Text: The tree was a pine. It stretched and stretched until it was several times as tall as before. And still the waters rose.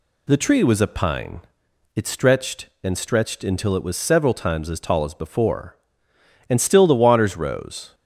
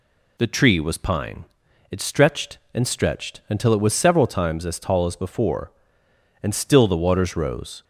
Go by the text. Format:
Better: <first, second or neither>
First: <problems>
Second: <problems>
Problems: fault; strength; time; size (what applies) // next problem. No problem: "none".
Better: first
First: none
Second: skips "a"; at 0.9 s